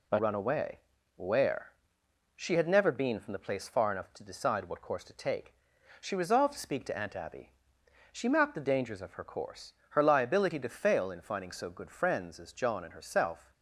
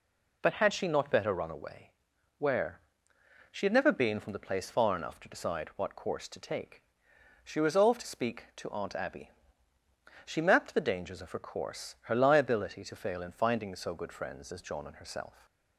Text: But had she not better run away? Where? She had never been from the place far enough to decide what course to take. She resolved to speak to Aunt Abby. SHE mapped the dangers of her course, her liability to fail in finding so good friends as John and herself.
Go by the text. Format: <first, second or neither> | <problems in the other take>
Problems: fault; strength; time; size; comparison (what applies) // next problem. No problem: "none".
second | skips "had she not better"; at 0.1 s